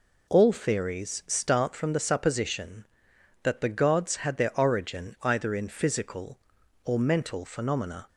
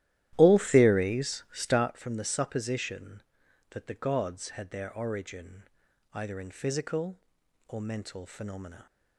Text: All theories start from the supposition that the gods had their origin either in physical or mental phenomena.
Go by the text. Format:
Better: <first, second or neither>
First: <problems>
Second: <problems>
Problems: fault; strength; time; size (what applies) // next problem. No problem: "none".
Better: first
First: none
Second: starts louder than the rest; strong; until 1.9 s; 13.5 dB // pauses between "origin" and "either"; noticeable; at 5.6 s; 0.50 s long